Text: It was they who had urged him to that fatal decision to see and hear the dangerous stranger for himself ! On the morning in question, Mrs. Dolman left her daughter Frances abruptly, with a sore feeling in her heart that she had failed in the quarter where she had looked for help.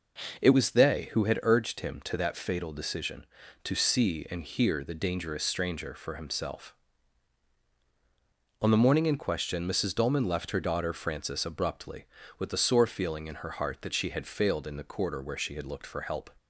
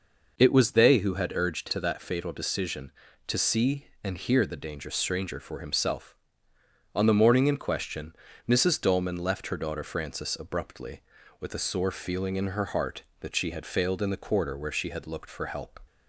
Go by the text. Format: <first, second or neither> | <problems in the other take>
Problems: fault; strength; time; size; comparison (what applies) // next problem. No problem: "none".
first | skips "him"; at 1.6 s